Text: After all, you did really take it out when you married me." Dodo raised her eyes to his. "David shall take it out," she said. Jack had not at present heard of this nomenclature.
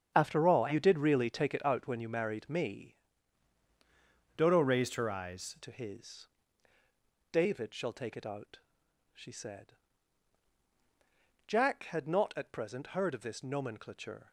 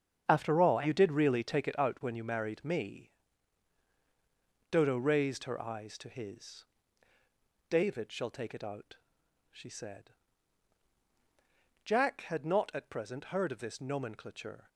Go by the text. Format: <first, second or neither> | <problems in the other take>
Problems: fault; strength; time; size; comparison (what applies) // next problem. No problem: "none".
second | starts louder than the rest; strong; until 1.1 s; 7.5 dB; strong in the second // changes voice from "Dodo" to "eyes"; from 4.3 to 5.5 s; 1.2 s long